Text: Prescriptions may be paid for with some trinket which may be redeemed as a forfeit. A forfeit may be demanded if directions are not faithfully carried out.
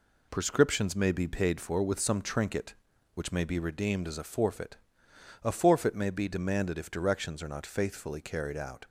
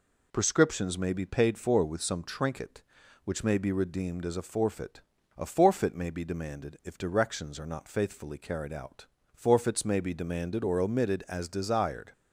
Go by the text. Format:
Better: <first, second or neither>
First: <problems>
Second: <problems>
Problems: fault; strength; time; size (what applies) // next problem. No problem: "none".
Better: first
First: none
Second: goes on to say "Forfeits may be demanded or omitted as desired"; strong; from 9.3 s on; 2.7 s long